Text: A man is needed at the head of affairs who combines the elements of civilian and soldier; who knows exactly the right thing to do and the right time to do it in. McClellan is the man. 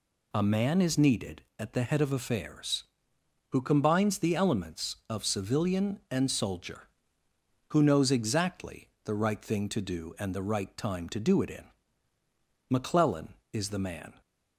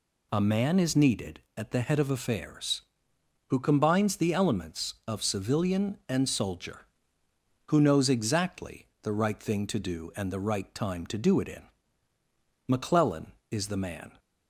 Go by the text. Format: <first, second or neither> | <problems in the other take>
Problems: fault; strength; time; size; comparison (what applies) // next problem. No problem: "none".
neither | pauses between "exactly" and "the"; slight; the same in both